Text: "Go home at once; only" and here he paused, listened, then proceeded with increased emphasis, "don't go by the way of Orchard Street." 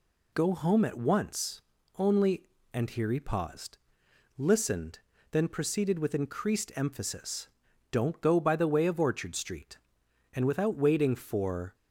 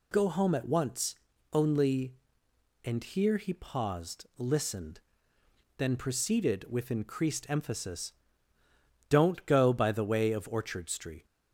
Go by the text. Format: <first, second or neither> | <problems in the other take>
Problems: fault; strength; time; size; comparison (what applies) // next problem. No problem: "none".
second | goes on to say "And without waiting for"; from 10.3 s on; 1.4 s long